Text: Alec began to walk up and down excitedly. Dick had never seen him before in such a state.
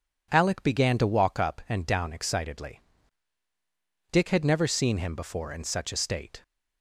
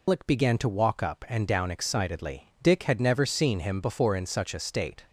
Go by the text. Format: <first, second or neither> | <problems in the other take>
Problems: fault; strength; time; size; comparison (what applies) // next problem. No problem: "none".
first | loses the start of "Alec"; at 0.0 s; 160 ms